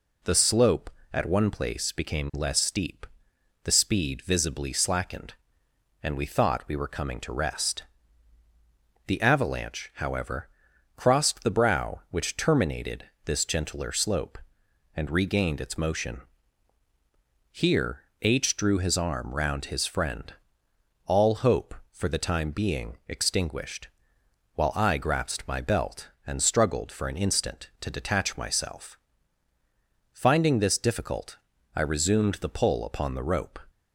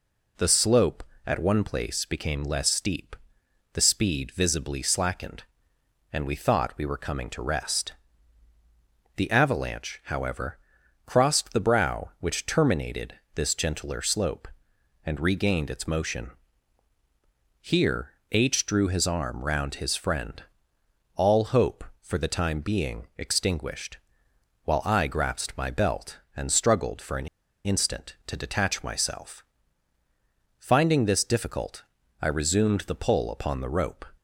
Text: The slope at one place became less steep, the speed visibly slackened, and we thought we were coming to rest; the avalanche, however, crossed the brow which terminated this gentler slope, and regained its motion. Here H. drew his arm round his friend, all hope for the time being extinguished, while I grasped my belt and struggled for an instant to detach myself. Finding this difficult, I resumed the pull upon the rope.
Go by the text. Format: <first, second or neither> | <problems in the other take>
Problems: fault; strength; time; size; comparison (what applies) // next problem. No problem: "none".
first | pauses between "terminated" and "this"; slight; at 13.1 s; 0.22 s long; slight in the first // pauses between "Here" and "H"; slight; at 18.1 s; 0.18 s long; slight in the first // pauses between "an" and "instant"; at 27.2 s; 0.37 s long